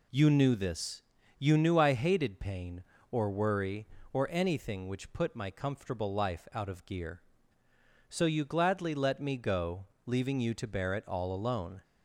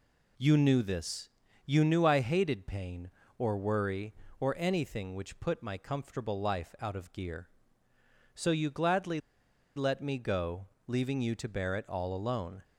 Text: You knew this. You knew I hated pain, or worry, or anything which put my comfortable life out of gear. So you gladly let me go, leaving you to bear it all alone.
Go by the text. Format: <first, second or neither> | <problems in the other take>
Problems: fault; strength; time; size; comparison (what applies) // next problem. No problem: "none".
first | pauses between "gladly" and "let"; noticeable; at 9.1 s; 0.56 s long